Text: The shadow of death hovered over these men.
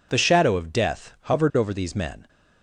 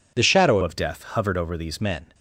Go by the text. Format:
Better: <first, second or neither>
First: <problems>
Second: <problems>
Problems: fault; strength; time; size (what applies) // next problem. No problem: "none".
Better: first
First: none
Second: changes voice from "of" to "these"; from 0.6 to 1.8 s; 1.2 s long